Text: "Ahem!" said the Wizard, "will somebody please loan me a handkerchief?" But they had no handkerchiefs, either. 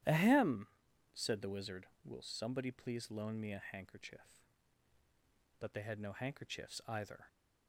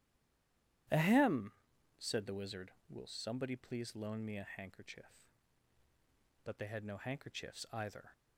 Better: first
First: starts louder than the rest; strong; until 1.5 s; 12 dB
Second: stays silent before the first word; slight; until 0.8 s; 0.8 s long // starts louder than the rest; strong; until 2.3 s; 12 dB

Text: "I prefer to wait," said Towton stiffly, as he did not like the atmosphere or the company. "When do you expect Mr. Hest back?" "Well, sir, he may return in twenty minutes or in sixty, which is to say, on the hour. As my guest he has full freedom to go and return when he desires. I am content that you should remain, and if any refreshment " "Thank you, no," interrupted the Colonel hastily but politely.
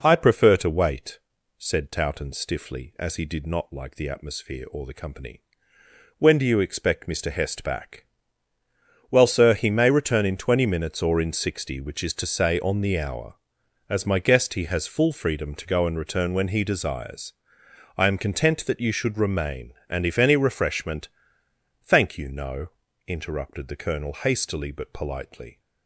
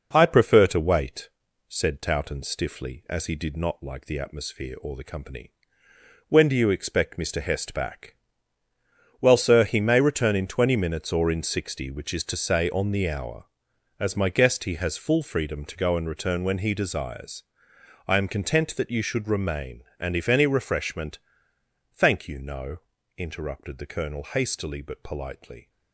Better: first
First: none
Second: gets quieter; noticeable; throughout; 6 dB

